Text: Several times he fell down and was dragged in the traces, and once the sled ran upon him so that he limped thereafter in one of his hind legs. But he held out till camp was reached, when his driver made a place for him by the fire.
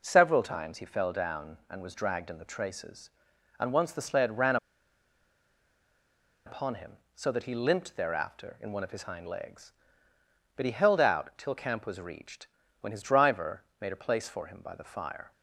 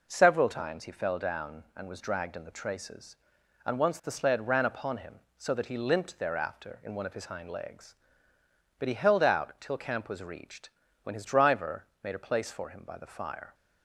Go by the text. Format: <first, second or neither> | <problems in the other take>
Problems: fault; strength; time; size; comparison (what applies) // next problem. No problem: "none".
second | pauses between "ran" and "upon"; strong; at 4.5 s; 1.9 s long // pauses between "driver" and "made"; slight; at 13.6 s; 0.18 s long; slight in the second